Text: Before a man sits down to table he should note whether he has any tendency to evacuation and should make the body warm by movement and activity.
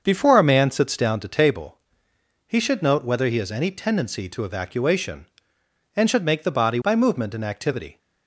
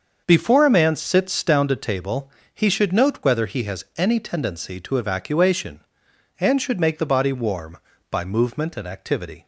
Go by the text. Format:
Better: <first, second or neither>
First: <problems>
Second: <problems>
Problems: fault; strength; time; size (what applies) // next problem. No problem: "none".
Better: second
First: starts louder than the rest; until 1.0 s; 6.5 dB // pauses between "table" and "he"; noticeable; at 1.7 s; 0.70 s long // skips "warm"; at 6.8 s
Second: starts louder than the rest; until 1.2 s; 6.5 dB // pauses between "table" and "he"; slight; at 2.2 s; 0.24 s long